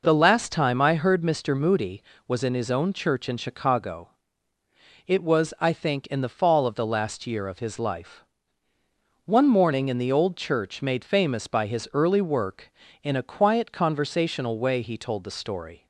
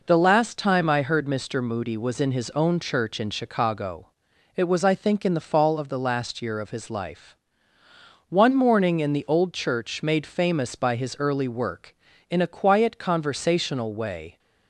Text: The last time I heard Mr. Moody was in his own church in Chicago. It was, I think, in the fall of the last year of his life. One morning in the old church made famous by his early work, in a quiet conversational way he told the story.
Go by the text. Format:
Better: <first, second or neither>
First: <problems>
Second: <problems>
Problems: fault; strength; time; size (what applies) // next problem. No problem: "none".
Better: first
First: none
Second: stops before "he told the story"; at 14.3 s